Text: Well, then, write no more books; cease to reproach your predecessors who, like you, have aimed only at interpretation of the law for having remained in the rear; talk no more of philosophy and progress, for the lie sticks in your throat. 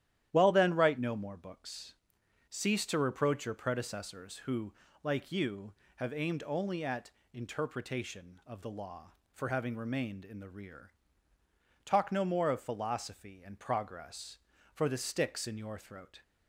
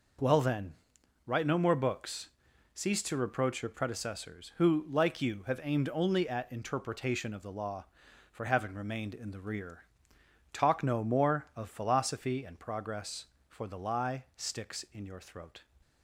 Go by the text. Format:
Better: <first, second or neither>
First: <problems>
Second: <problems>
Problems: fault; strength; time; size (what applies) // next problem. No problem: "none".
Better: second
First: starts louder than the rest; strong; until 1.3 s; 11.5 dB // pauses between "at" and "interpretation"; slight; at 7.1 s; 0.22 s long // skips "lie"; at 14.9 s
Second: none